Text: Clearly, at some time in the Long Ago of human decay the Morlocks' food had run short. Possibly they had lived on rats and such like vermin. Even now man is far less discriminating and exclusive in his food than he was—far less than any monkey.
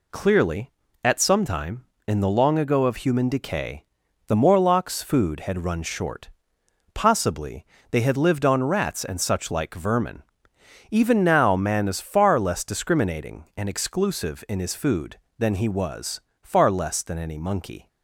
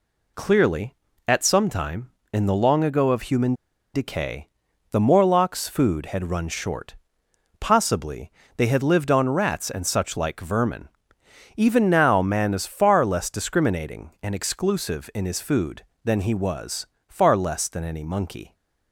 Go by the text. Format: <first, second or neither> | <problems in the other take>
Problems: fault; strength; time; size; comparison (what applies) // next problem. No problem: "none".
first | pauses between "human" and "decay"; at 3.5 s; 0.40 s long // pauses between "decay" and "the"; at 4.4 s; 0.42 s long; also in the first // pauses between "Possibly" and "they"; slight; at 8.2 s; 0.26 s long; slight in the first